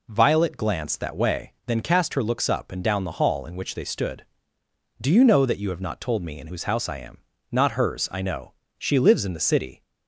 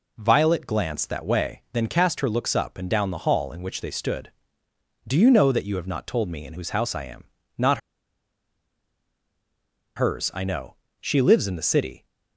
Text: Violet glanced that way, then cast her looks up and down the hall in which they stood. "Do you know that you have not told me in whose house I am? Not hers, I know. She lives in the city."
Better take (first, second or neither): first